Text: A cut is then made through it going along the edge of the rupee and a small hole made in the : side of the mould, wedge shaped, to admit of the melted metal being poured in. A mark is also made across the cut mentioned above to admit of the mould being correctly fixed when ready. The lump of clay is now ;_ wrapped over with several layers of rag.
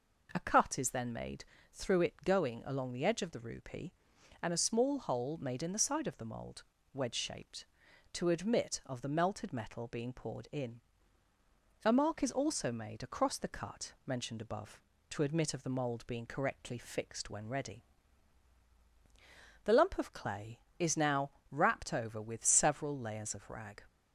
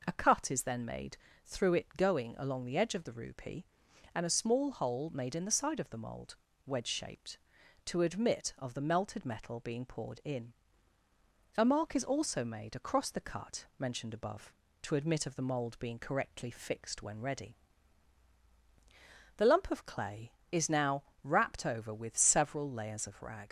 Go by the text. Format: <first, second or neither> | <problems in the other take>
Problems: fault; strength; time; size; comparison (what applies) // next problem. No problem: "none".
first | pauses between "made" and "through"; slight; at 1.1 s; 0.28 s long; slight in the first // leaves "rag" unfinished; at 23.4 s; 85 ms